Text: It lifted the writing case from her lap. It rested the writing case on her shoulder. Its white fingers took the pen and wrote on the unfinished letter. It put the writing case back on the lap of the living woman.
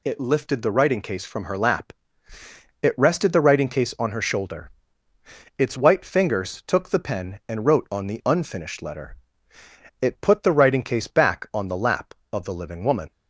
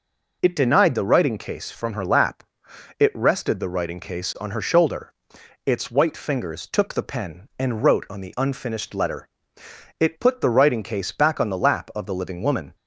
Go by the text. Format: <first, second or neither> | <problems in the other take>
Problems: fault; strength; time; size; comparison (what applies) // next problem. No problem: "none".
first | says "denied" for "lifted"; at 0.5 s